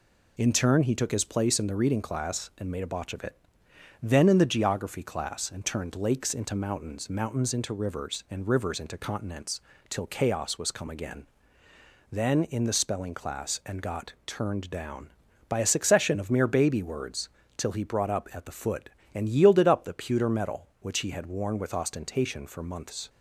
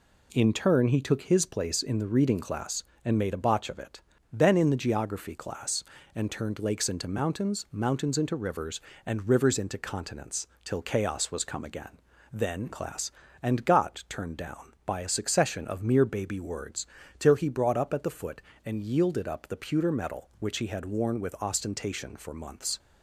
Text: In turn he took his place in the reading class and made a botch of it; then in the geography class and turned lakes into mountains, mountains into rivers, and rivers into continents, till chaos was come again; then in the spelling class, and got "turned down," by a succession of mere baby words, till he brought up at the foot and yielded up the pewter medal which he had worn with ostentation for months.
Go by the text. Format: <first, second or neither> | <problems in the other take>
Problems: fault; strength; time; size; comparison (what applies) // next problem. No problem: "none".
first | skips "in the spelling"; at 12.7 s